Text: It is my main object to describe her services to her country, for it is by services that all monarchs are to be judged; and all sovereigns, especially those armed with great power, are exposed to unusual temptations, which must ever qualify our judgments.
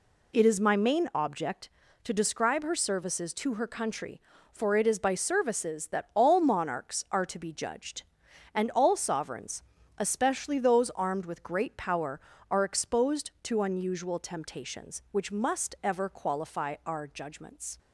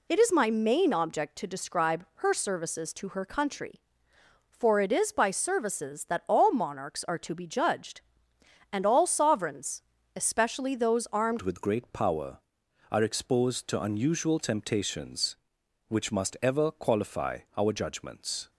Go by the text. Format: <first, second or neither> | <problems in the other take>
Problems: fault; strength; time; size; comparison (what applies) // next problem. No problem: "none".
first | changes voice at "with"; from 11.4 s on; 7.1 s long // pauses between "qualify" and "our"; slight; at 17.3 s; 0.18 s long